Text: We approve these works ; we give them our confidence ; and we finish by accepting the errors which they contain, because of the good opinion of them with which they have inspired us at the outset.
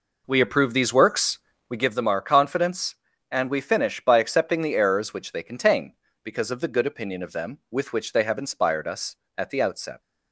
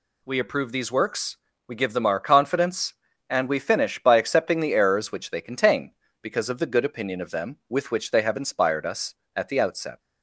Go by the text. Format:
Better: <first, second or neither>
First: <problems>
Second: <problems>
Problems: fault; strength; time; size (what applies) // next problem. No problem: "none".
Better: second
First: starts louder than the rest; noticeable; until 1.9 s; 4.5 dB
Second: none